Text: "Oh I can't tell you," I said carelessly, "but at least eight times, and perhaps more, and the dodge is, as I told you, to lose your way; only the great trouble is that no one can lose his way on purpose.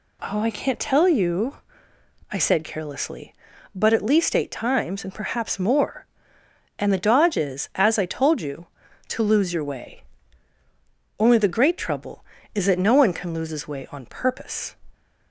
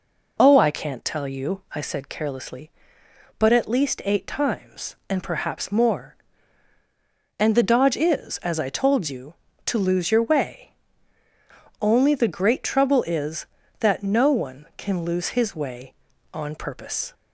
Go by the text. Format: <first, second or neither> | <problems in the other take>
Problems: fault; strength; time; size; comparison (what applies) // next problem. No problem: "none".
neither | none